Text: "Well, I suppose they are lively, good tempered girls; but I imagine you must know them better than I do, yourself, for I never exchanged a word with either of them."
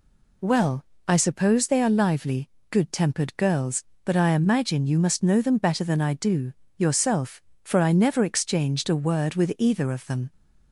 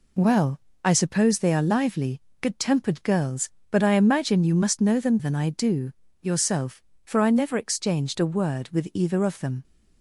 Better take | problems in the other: first | skips "better"; at 5.1 s

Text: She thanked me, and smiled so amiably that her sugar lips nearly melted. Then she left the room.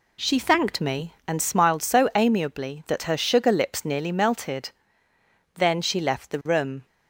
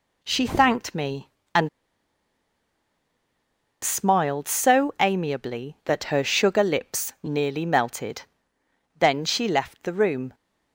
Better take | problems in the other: first | pauses between "and" and "smiled"; strong; at 1.6 s; 2.1 s long

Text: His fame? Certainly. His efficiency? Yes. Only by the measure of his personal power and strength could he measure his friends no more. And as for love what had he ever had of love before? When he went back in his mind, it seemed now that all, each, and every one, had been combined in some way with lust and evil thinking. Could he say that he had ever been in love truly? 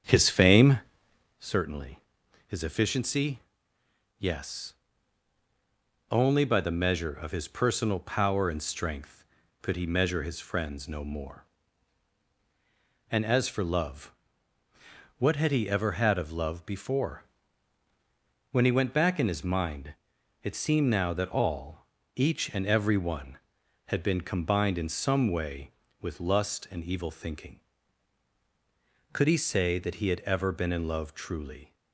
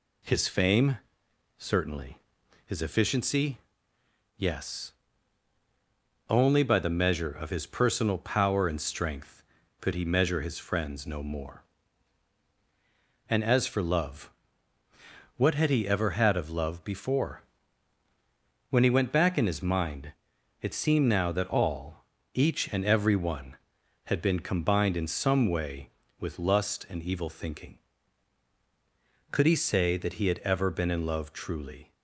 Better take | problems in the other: second | starts louder than the rest; strong; until 1.5 s; 8 dB // pauses between "love" and "what"; at 14.1 s; 1.0 s long; also in the second

